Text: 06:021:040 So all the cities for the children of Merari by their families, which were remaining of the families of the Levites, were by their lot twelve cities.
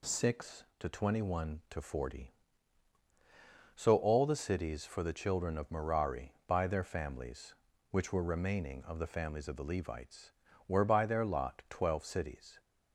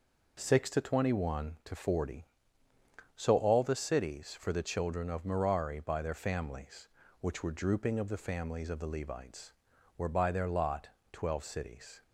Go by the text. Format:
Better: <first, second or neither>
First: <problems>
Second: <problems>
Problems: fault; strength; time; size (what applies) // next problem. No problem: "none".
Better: first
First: none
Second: says "drooping" for "remaining"; at 7.5 s // pauses between "lot" and "twelve"; slight; at 10.9 s; 0.22 s long